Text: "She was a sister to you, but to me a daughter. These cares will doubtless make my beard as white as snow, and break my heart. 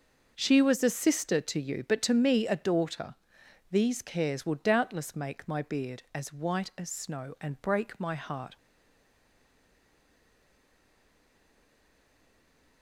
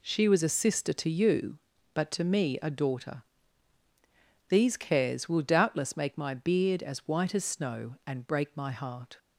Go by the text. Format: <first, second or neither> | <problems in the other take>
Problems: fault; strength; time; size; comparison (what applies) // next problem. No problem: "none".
second | starts louder than the rest; noticeable; until 1.3 s; 6 dB // stays silent after the last word; strong; from 8.5 s on; 4.3 s long